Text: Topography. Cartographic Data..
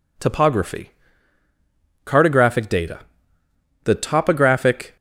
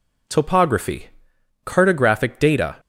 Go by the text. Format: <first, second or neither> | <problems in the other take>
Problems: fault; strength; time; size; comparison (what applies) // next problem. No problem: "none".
second | goes on to say "The topographic"; noticeable; from 3.8 s on; 1.1 s long